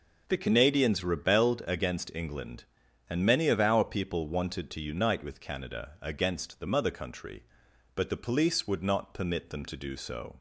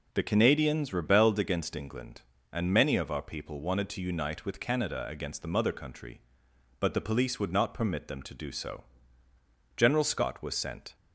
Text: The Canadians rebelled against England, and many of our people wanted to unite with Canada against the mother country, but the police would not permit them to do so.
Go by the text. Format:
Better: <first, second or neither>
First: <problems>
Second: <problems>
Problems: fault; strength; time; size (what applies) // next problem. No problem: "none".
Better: first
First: none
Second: goes on to say "General Scott was sent"; noticeable; from 9.7 s on; 1.1 s long